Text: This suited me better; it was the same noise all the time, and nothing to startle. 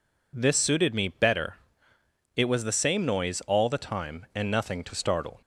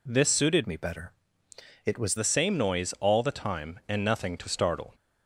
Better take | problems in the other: first | changes voice from "me" to "was"; from 0.6 to 2.1 s; 1.5 s long

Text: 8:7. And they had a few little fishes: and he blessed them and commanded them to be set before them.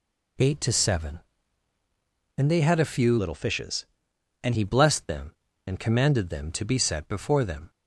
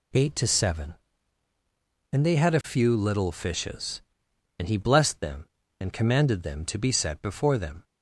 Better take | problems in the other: second | changes voice from "little" to "and"; from 3.1 to 4.5 s; 1.4 s long

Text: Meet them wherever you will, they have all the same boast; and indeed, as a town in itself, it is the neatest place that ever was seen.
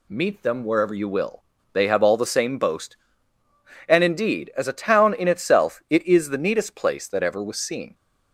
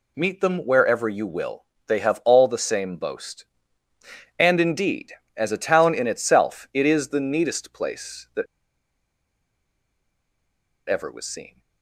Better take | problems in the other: first | pauses between "that" and "ever"; strong; at 8.4 s; 2.4 s long

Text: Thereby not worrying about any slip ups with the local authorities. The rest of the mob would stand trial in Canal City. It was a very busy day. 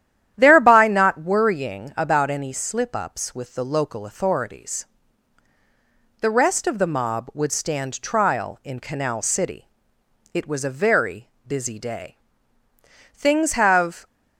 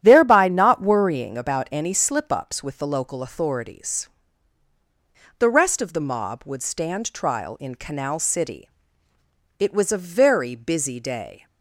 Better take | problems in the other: second | starts louder than the rest; strong; until 1.3 s; 11 dB; strong in the second // goes on to say "Things have"; noticeable; from 13.1 s on; 0.92 s long

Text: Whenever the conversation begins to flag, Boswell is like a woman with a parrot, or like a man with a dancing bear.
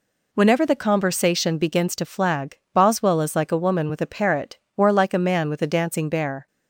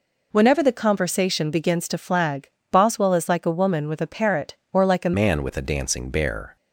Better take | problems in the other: first | changes voice at "man"; from 5.1 s on; 1.4 s long

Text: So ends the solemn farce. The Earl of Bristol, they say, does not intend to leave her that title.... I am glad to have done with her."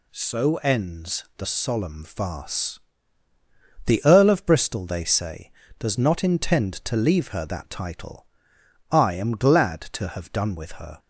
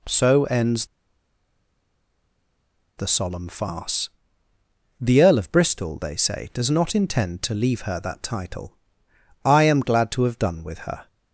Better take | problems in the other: first | pauses between "ends" and "the"; strong; at 0.8 s; 2.1 s long

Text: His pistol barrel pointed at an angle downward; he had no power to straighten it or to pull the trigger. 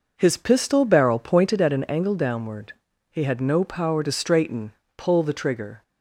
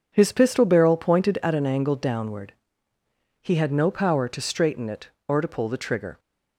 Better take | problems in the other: second | skips "it or to"; at 4.8 s

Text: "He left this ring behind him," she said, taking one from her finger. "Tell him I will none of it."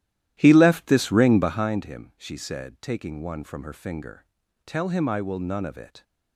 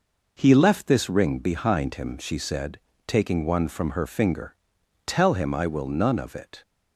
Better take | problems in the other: second | starts louder than the rest; strong; until 1.7 s; 13 dB

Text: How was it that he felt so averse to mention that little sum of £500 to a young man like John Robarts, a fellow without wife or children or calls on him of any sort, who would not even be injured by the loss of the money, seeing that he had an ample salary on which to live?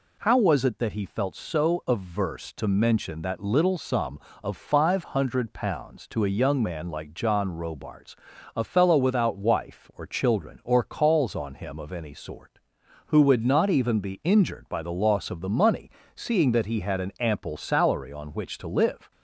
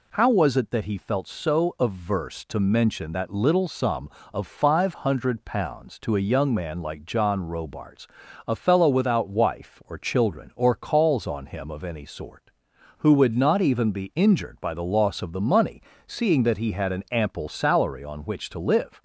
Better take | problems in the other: neither | none

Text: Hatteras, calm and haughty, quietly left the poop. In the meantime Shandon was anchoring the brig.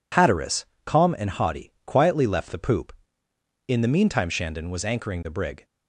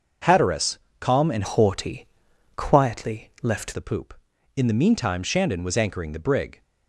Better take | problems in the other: first | changes voice from "haughty" to "left"; from 1.4 to 3.7 s; 2.3 s long

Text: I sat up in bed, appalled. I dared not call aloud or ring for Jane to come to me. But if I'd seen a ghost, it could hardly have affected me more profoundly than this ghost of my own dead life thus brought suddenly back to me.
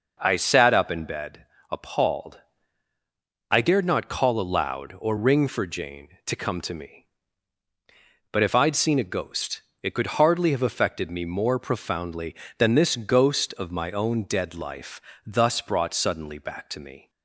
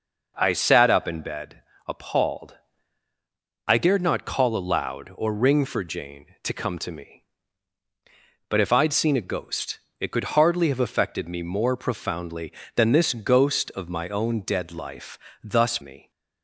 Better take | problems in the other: first | pauses between "life" and "thus"; slight; at 15.1 s; 0.24 s long; slight in the first // skips "brought suddenly back to"; at 15.7 s

